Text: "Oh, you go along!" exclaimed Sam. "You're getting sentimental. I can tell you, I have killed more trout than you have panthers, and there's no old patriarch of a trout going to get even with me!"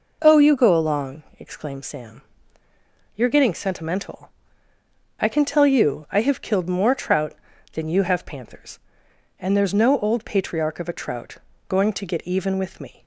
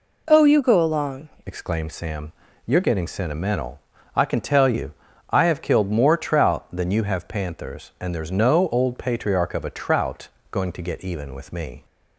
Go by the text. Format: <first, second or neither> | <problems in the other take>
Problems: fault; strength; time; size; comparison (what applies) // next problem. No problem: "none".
first | changes voice at "exclaimed"; from 1.4 s on; 10.4 s long // pauses between "trout" and "going"; slight; at 10.2 s; 0.24 s long; slight in the first